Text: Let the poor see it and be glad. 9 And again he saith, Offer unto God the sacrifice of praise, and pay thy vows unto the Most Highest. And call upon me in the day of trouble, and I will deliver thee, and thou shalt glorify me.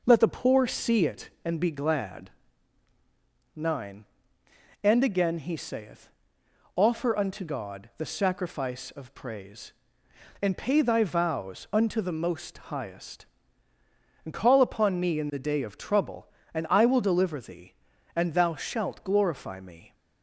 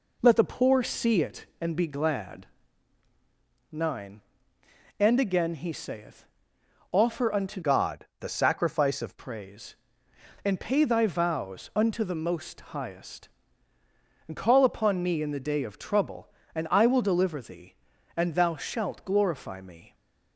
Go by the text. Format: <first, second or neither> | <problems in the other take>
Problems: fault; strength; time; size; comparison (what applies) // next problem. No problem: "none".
first | changes voice from "God" to "of"; from 7.6 to 9.1 s; 1.5 s long